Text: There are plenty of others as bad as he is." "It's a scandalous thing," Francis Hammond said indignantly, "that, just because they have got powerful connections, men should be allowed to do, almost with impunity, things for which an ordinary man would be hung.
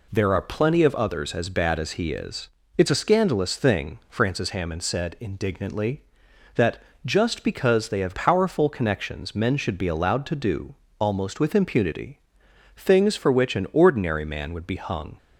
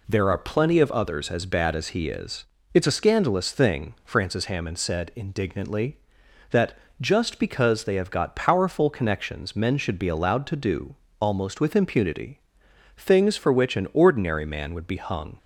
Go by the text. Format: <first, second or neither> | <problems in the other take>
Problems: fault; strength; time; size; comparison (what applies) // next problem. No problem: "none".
second | skips "got"; at 8.1 s